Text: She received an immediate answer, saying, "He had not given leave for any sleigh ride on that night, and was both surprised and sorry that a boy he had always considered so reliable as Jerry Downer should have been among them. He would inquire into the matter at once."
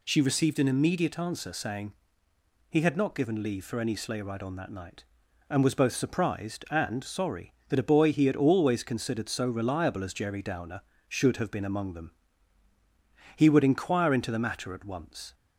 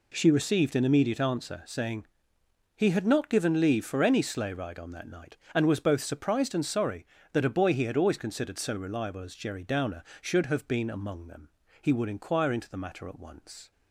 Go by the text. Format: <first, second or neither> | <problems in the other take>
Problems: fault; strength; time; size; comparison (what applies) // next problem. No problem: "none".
neither | none